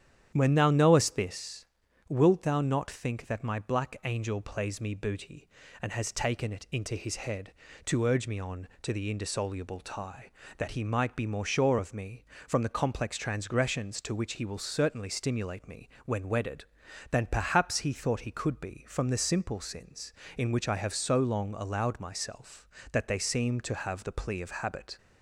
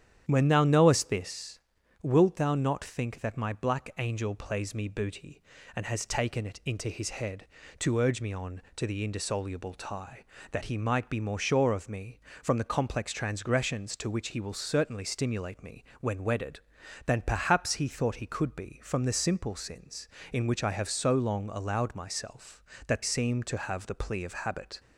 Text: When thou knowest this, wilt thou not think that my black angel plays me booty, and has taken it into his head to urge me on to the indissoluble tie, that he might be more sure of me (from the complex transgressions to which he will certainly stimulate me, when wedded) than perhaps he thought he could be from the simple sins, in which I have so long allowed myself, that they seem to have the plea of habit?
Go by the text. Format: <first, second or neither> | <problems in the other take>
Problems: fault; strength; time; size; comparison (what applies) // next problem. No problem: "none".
first | starts louder than the rest; strong; until 1.2 s; 9.5 dB; strong in the first // skips "they"; at 23.0 s